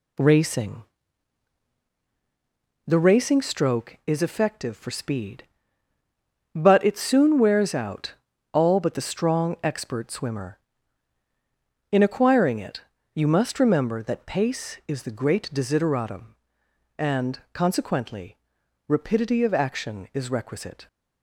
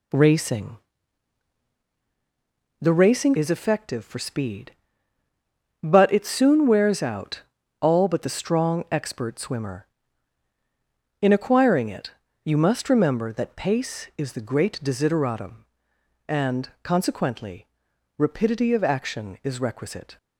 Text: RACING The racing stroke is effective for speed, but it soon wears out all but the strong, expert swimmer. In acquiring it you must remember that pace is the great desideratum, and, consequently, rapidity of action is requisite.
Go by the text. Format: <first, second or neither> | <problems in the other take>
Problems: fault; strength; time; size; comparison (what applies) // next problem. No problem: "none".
first | pauses between "RACING" and "The"; strong; at 0.7 s; 2.0 s long; strong in the first // skips "stroke"; at 3.3 s // pauses between "out" and "all"; slight; at 7.4 s; 0.36 s long; slight in the first // pauses between "it" and "you"; slight; at 12.0 s; 0.34 s long; slight in the first